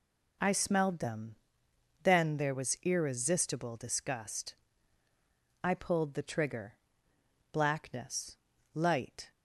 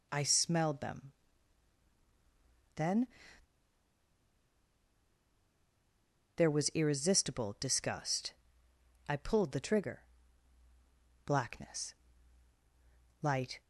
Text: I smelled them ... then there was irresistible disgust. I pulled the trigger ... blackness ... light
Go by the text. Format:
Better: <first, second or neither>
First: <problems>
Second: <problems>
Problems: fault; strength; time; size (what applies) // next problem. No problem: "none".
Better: first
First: none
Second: pauses between "then" and "there"; strong; at 3.0 s; 3.3 s long